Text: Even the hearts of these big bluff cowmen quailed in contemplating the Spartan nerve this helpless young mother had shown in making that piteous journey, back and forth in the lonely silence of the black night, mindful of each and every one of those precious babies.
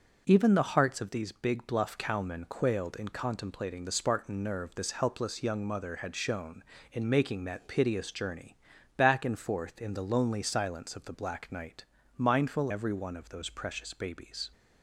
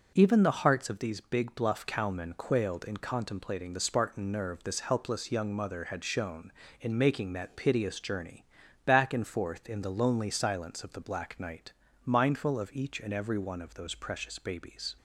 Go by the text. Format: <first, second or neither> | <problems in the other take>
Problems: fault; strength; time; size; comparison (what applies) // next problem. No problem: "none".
second | starts louder than the rest; until 1.2 s; 6.5 dB; also in the second // skips "of each and"; at 12.7 s